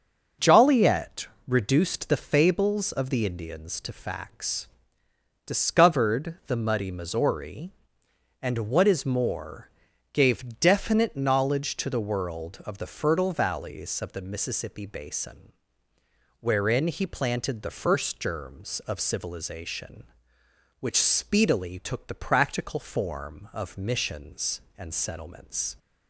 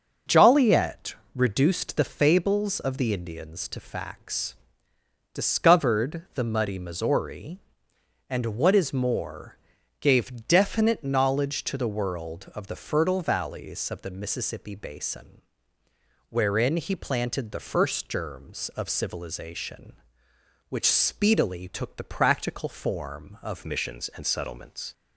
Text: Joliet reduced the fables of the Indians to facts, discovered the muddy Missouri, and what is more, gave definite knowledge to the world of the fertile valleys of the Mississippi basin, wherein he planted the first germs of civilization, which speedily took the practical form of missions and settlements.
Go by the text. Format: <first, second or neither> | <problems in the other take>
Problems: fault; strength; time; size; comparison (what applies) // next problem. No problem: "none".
first | starts louder than the rest; until 1.4 s; 6.5 dB; also in the first // pauses between "Joliet" and "reduced"; slight; at 1.1 s; 0.18 s long; slight in the first // changes voice at "missions"; from 23.6 s on; 1.3 s long